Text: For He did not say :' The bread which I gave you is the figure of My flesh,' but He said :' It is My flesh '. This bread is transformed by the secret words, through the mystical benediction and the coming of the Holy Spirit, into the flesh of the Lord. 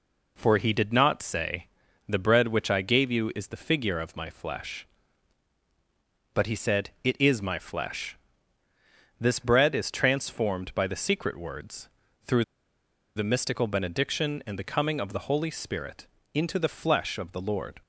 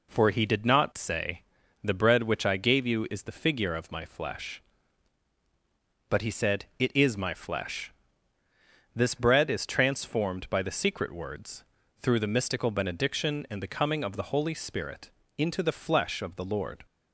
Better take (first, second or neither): second